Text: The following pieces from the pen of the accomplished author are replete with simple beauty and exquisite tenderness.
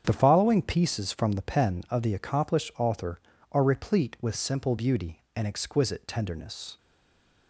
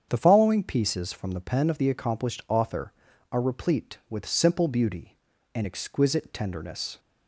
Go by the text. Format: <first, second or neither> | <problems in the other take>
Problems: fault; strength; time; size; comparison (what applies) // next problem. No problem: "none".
second | starts louder than the rest; strong; until 1.0 s; 8 dB; strong in the second // stays silent after the last word; slight; from 6.7 s on; 0.7 s long